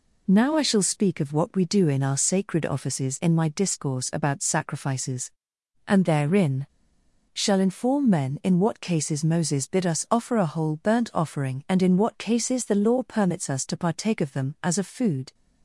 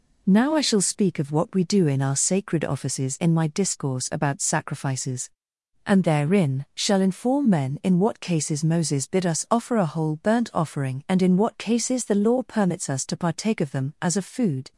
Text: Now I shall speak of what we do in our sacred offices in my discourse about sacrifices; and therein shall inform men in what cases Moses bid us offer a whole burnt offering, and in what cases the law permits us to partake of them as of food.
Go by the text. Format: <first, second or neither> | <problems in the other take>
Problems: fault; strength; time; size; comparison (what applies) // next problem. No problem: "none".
second | pauses between "therein" and "shall"; noticeable; at 6.6 s; 0.65 s long